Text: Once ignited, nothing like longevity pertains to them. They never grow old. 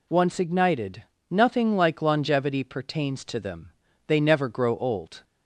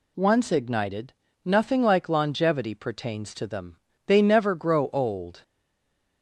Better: first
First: none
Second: stays silent after the last word; slight; from 5.4 s on; 0.8 s long

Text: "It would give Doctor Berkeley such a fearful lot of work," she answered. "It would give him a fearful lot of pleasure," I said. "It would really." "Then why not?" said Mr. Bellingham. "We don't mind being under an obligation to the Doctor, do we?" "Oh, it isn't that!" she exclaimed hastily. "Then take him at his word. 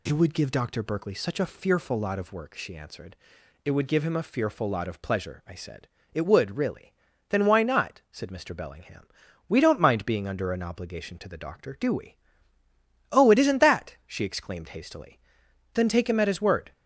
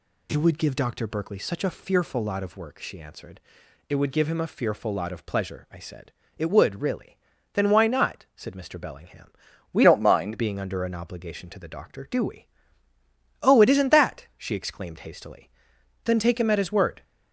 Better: first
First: none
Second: changes voice from "don't" to "mind"; from 9.8 to 10.3 s; 0.5 s long

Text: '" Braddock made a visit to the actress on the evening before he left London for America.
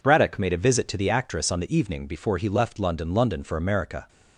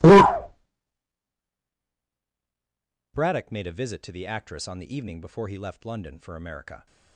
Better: second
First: says "London" twice; at 3.1 s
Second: none

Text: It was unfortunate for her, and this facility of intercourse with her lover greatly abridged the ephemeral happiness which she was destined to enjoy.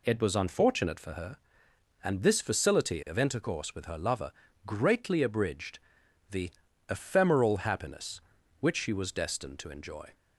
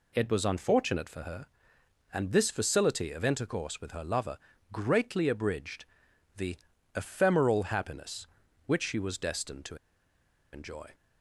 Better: first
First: pauses between "lover" and "greatly"; slight; at 4.3 s; 0.34 s long // pauses between "abridged" and "the"; noticeable; at 5.7 s; 0.52 s long // pauses between "the" and "ephemeral"; at 6.4 s; 0.40 s long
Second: pauses between "lover" and "greatly"; slight; at 4.3 s; 0.34 s long // pauses between "abridged" and "the"; noticeable; at 5.8 s; 0.52 s long // pauses between "the" and "ephemeral"; at 6.5 s; 0.40 s long // pauses between "to" and "enjoy"; noticeable; at 9.7 s; 0.76 s long

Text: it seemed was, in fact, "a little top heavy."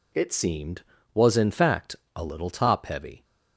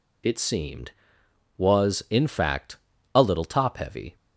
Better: neither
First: none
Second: none

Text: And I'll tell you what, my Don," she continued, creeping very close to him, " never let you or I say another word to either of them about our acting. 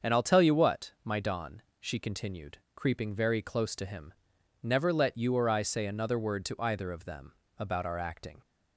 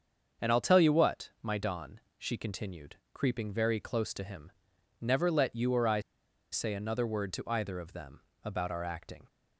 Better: first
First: starts louder than the rest; until 1.1 s; 7 dB // pauses between "them" and "about"; slight; at 7.3 s; 0.26 s long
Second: starts louder than the rest; until 1.5 s; 7 dB // pauses between "I" and "say"; noticeable; at 6.0 s; 0.51 s long // pauses between "them" and "about"; slight; at 8.2 s; 0.24 s long

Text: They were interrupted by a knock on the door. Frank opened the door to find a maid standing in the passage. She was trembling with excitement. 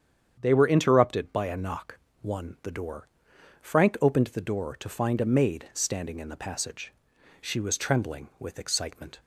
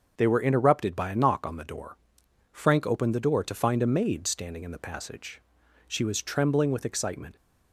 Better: second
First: starts louder than the rest; strong; until 1.4 s; 8.5 dB // says "one" for "on"; at 2.2 s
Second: starts louder than the rest; until 1.1 s; 6.5 dB

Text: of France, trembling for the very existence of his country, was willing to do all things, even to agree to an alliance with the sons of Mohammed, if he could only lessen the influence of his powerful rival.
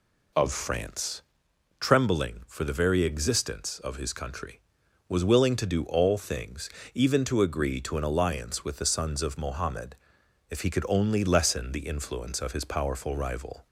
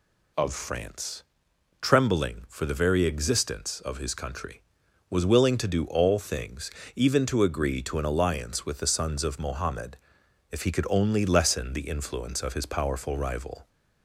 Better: second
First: starts louder than the rest; slight; until 1.5 s; 2.5 dB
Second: none

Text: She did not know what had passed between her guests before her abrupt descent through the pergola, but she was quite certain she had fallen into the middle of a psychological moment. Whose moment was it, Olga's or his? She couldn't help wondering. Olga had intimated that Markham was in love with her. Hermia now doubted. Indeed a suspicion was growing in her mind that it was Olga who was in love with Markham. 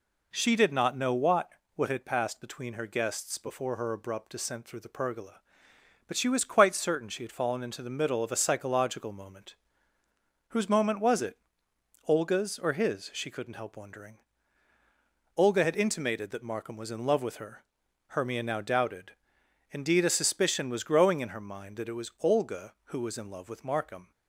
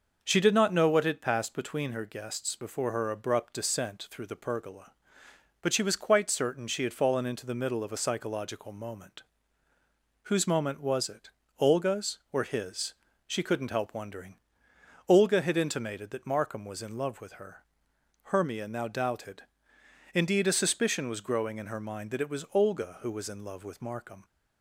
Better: second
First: says "what" twice; at 1.7 s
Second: none

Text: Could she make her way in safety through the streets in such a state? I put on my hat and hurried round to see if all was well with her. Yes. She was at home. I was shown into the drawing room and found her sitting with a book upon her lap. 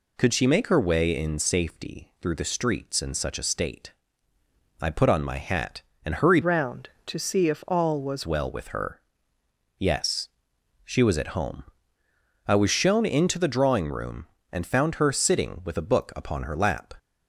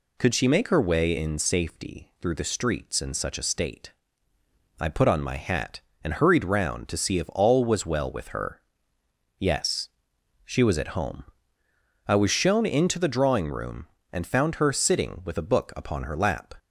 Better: second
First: changes voice from "round" to "was"; from 6.4 to 8.2 s; 1.8 s long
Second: none

